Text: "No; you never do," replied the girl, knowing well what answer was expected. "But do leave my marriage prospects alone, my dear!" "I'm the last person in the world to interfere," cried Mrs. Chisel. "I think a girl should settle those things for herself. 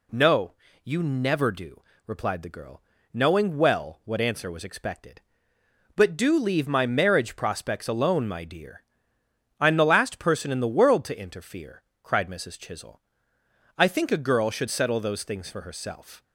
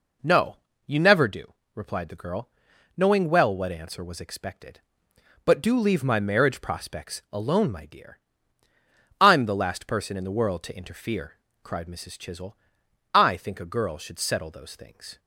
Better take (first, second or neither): first